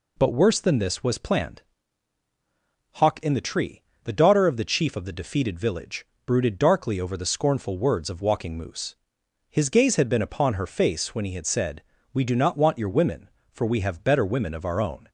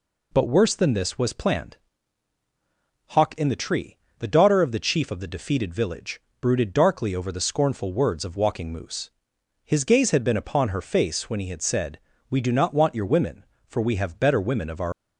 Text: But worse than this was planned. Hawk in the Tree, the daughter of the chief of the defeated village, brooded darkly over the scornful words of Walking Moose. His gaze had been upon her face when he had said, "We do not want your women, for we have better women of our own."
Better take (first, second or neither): first